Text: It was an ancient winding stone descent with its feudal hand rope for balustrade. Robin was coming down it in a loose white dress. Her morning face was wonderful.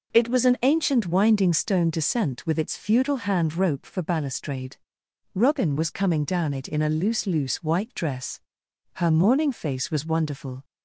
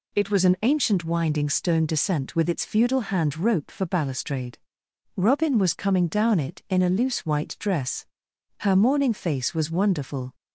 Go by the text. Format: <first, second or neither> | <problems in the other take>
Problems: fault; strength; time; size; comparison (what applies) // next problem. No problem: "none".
second | says "loose" twice; at 7.2 s